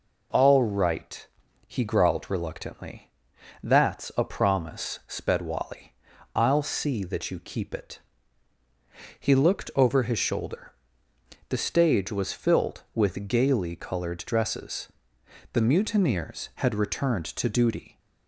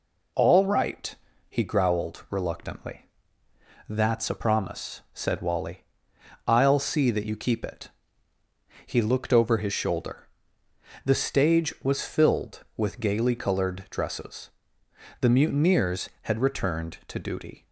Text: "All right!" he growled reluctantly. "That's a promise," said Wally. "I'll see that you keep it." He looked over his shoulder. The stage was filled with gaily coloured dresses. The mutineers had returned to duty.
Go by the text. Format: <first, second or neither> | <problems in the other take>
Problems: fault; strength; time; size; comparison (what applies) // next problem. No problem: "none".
second | says "sped" for "said"; at 5.0 s